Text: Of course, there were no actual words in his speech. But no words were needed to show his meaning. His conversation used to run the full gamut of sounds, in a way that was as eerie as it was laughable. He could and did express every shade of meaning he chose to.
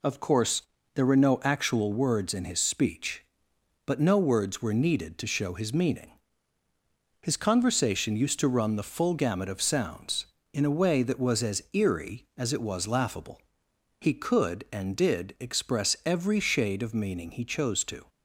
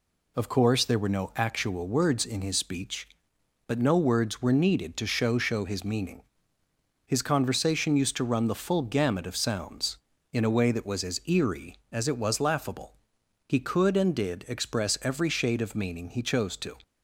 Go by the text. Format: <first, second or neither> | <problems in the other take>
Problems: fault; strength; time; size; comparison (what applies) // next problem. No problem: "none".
first | says "show" twice; at 5.3 s